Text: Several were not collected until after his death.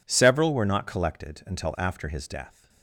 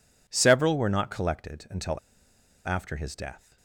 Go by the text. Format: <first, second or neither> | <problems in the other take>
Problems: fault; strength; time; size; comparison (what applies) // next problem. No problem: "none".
first | pauses between "until" and "after"; noticeable; at 1.9 s; 0.69 s long